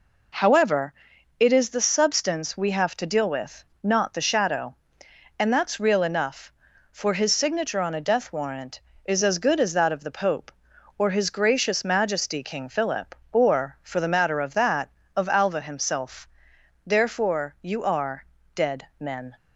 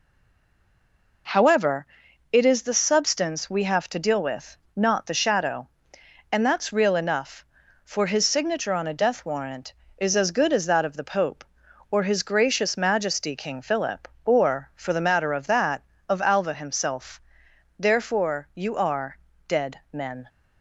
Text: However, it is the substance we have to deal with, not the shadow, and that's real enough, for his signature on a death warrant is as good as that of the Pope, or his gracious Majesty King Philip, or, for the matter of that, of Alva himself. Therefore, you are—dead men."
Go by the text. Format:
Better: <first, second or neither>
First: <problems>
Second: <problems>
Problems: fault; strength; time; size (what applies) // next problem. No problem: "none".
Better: first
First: none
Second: stays silent before the first word; noticeable; until 1.2 s; 1.2 s long